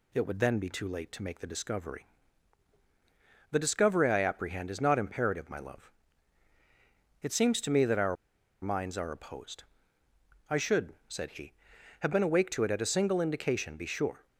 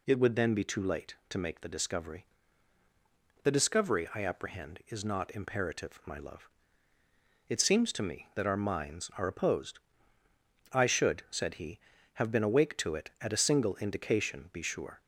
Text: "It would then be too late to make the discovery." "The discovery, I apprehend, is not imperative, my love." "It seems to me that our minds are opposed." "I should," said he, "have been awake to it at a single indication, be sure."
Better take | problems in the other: second | pauses between "our" and "minds"; noticeable; at 8.1 s; 0.46 s long

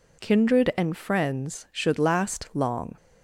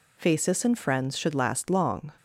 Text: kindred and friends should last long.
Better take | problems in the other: first | says "phasis" for "kindred"; at 0.1 s

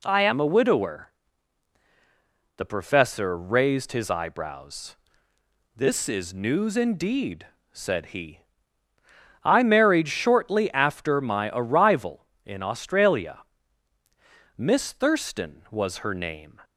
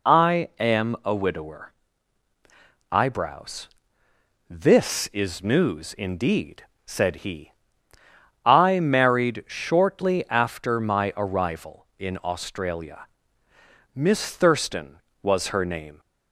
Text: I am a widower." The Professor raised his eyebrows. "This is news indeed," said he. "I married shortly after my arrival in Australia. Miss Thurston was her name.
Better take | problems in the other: first | skips "The Professor raised his"; at 2.3 s

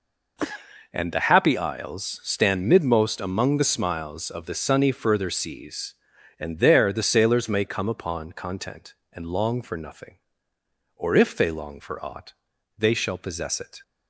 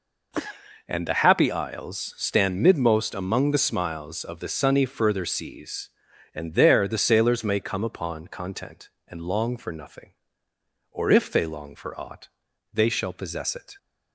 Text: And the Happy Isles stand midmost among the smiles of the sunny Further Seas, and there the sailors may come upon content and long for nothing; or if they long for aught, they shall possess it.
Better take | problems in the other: neither | none

